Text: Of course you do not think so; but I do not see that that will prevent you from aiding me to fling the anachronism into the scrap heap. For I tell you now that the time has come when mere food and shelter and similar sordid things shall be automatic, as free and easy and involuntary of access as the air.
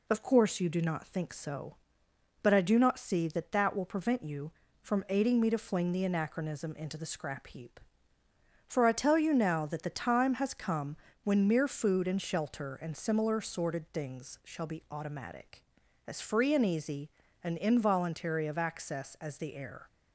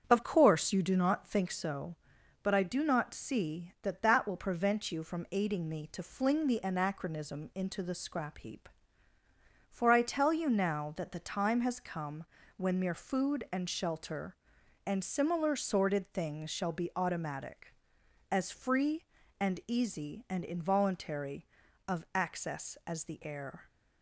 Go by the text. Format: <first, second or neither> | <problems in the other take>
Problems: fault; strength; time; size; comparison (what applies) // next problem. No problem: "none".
first | starts louder than the rest; strong; until 1.6 s; 7 dB // pauses between "come" and "when"; slight; at 12.2 s; 0.32 s long; slight in the first